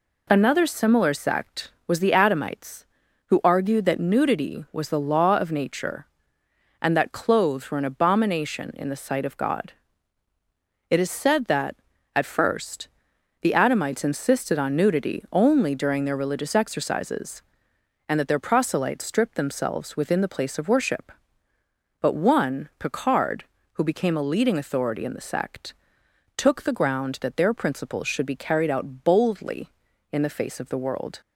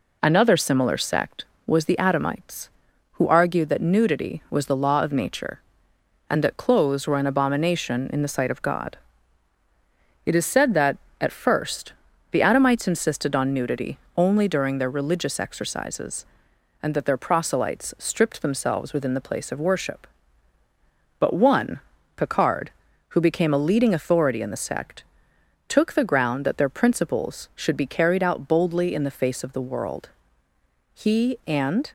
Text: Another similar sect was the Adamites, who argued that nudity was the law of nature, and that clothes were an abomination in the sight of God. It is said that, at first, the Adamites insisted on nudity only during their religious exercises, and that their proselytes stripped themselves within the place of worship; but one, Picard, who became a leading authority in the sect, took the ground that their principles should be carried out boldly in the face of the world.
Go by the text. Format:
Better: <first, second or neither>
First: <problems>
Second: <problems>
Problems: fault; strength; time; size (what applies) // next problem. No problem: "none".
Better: first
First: none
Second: pauses between "nudity" and "only"; slight; at 13.9 s; 0.18 s long // goes on to say "He and"; noticeable; from 30.9 s on; 1.0 s long